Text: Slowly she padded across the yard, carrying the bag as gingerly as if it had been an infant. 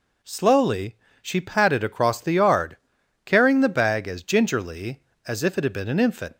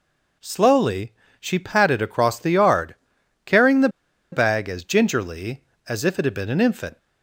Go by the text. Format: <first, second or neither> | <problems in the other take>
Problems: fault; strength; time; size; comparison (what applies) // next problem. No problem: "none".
first | pauses between "Slowly" and "she"; slight; at 1.1 s; 0.28 s long; slight in the first // pauses between "the" and "bag"; at 3.8 s; 0.43 s long